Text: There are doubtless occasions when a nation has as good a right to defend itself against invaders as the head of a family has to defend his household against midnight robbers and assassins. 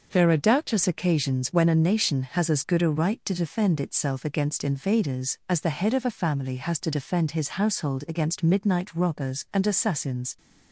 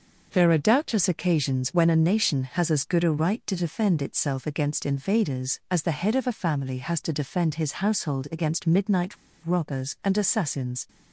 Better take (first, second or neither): first